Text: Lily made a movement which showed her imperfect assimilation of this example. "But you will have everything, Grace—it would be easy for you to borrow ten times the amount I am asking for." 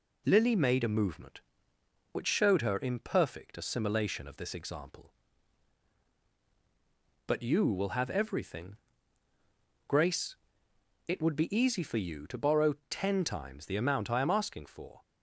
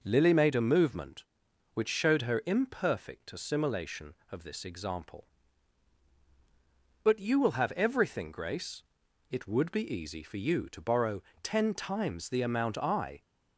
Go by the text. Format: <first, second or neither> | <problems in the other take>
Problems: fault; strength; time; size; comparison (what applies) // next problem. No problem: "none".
first | pauses between "borrow" and "ten"; slight; at 11.2 s; 0.22 s long; slight in the first // stops before "am asking for"; at 13.2 s